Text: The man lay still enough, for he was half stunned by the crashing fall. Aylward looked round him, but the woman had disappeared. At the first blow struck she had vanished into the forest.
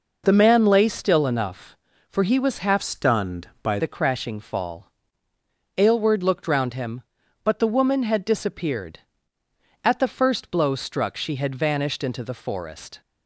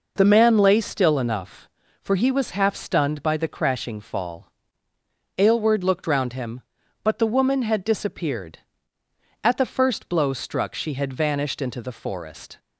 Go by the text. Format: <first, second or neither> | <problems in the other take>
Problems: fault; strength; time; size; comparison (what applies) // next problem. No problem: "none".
second | changes voice from "stunned" to "by"; from 2.8 to 3.7 s; 0.9 s long